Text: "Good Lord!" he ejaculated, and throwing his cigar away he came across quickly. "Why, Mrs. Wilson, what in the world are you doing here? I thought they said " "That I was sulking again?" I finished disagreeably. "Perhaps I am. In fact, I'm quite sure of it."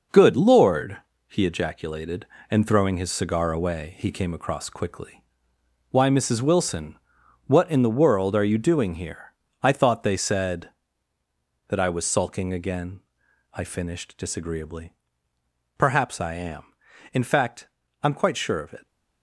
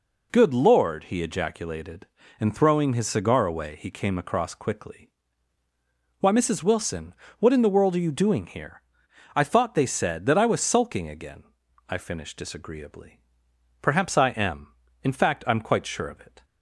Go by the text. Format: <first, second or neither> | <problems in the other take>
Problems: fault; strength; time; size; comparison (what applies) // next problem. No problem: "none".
second | gets quieter; strong; throughout; 10 dB